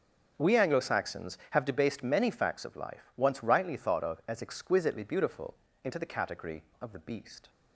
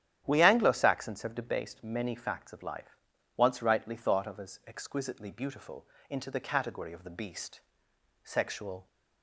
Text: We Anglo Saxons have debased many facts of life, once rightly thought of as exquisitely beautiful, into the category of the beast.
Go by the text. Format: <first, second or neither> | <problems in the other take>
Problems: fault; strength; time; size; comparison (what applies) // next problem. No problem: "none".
first | starts louder than the rest; strong; until 1.2 s; 9.5 dB // goes on to say "Sexual"; noticeable; from 8.2 s on; 0.64 s long